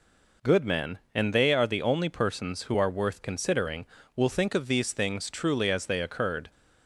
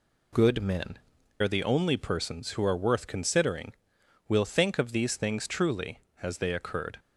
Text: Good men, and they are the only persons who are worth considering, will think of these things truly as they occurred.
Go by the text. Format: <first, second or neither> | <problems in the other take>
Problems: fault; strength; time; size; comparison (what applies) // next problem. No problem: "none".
first | skips "and they"; at 1.1 s